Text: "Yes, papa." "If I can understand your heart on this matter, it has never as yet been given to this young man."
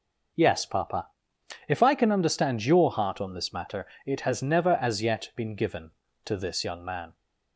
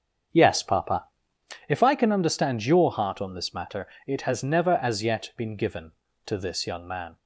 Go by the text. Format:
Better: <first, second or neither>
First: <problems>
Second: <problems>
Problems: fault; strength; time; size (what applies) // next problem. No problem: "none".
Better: first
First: none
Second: starts louder than the rest; strong; until 1.5 s; 7.5 dB